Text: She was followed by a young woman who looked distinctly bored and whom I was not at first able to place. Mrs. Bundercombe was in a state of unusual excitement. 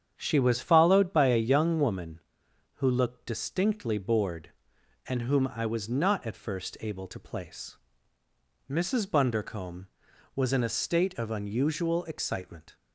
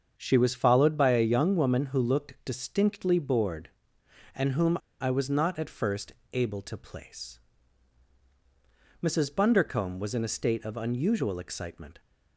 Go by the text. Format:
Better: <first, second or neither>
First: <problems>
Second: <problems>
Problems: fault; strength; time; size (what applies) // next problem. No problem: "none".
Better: first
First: starts louder than the rest; strong; until 1.1 s; 8.5 dB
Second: starts louder than the rest; until 1.1 s; 7 dB // pauses between "whom" and "I"; slight; at 4.7 s; 0.22 s long // pauses between "first" and "able"; slight; at 6.1 s; 0.20 s long